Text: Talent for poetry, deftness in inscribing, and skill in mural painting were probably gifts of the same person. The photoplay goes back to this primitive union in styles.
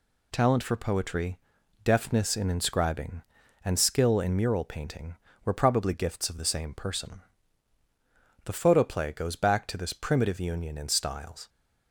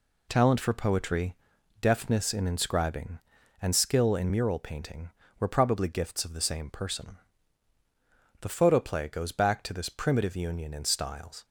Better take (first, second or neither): first